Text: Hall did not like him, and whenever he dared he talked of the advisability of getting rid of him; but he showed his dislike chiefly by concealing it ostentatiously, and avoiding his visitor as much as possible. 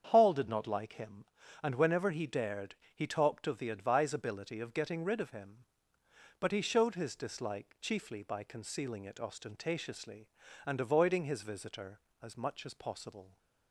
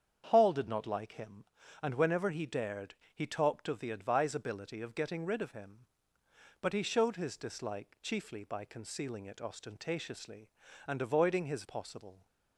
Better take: first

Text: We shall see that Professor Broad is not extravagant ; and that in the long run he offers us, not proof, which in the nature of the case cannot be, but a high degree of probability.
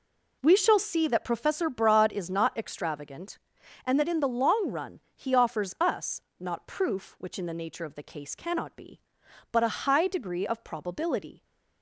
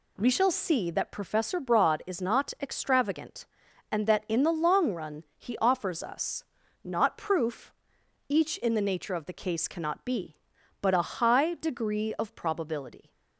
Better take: first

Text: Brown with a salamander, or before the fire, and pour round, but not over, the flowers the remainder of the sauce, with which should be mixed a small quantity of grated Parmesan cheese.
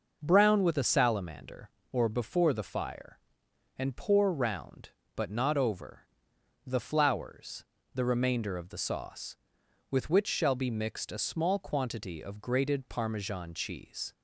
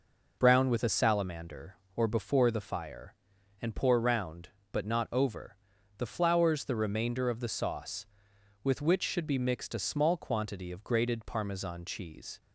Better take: second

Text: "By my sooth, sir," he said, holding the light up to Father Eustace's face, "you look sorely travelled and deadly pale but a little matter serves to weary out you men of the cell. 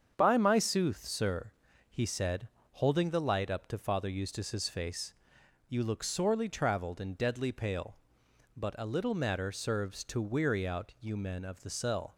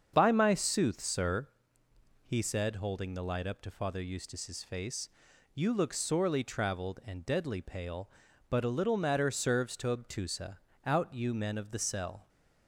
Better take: first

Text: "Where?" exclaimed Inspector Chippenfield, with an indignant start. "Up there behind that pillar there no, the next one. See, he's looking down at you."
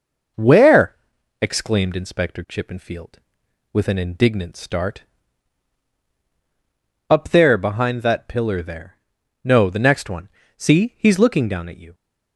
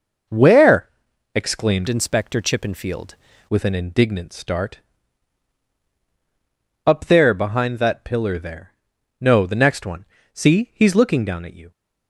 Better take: first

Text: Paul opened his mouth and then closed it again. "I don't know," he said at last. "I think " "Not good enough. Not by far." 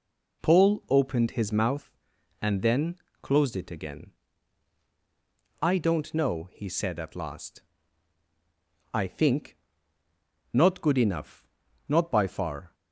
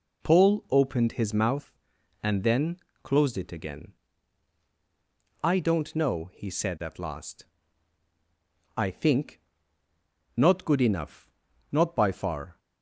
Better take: neither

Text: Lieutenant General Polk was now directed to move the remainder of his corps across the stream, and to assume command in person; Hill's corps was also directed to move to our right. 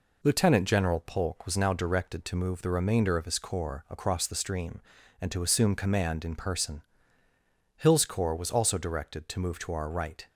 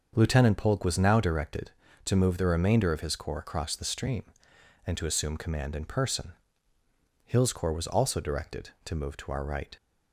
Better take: first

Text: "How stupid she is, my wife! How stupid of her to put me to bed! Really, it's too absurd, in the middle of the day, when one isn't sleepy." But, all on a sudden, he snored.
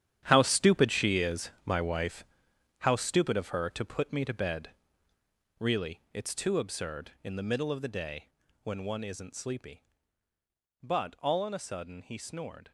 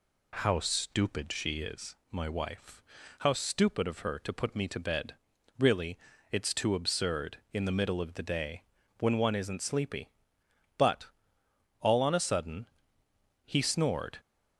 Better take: second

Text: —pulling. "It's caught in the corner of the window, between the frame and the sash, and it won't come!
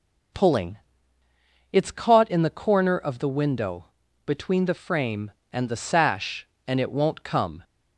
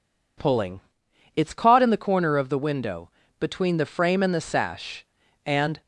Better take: first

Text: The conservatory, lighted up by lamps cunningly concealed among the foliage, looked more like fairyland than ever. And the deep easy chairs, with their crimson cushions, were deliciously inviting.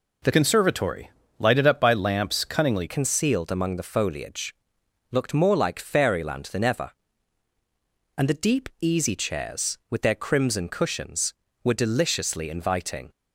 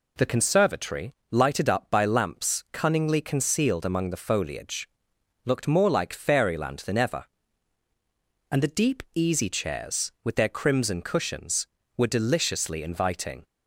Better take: second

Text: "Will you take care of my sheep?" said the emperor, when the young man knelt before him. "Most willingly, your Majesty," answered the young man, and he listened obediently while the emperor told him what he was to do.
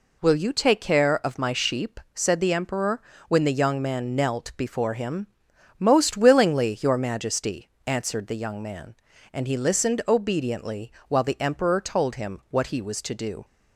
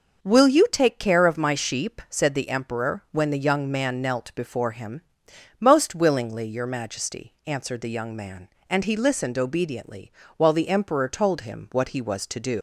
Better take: first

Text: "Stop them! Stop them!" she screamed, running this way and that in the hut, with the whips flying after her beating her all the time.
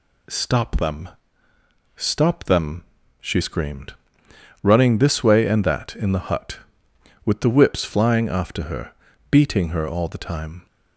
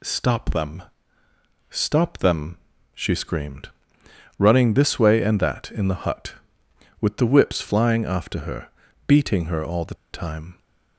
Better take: first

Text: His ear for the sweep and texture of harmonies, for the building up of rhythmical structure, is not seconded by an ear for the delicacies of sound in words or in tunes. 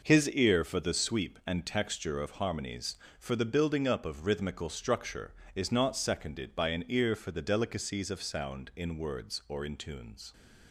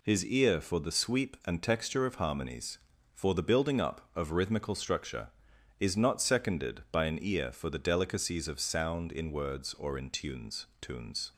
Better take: first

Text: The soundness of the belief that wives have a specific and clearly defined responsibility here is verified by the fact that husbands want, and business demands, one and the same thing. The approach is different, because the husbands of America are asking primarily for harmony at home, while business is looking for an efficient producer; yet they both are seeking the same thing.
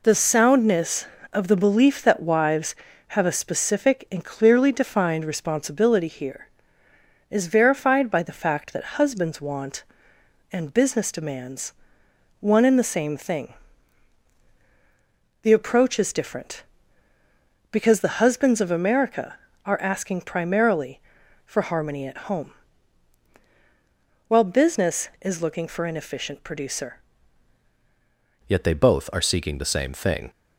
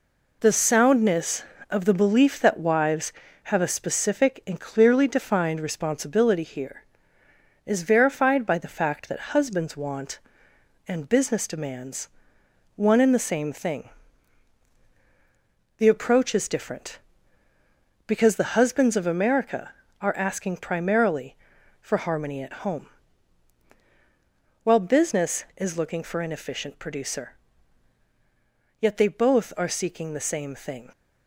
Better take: second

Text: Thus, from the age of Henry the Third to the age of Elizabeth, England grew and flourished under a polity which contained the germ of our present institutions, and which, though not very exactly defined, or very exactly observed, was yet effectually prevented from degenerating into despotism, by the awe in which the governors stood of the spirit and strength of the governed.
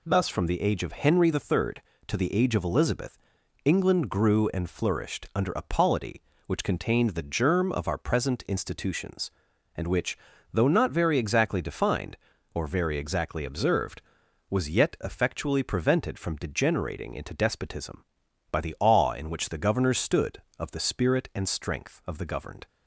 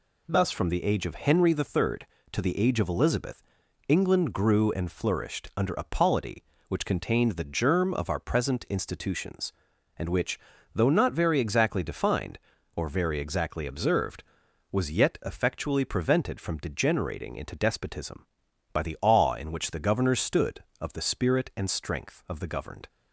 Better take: neither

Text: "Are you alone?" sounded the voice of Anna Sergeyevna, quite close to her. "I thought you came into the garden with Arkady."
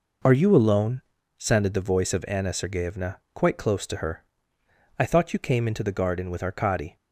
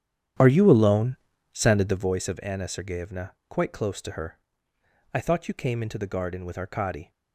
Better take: first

